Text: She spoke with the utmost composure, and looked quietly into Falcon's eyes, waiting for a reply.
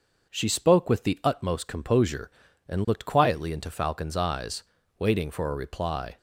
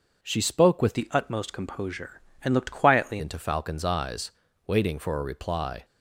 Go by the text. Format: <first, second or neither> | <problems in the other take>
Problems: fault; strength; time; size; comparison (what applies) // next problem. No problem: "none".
first | changes voice from "the" to "quietly"; from 0.9 to 3.1 s; 2.2 s long